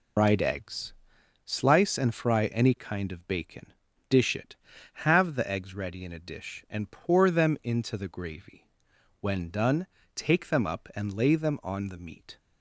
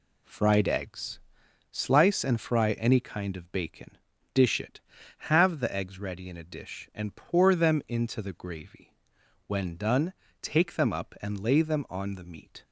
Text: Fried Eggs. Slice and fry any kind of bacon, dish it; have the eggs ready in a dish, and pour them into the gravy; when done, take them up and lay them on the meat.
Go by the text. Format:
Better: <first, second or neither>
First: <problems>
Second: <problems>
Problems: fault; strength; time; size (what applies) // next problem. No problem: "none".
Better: second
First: loses the start of "Fried"; at 0.1 s; 185 ms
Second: none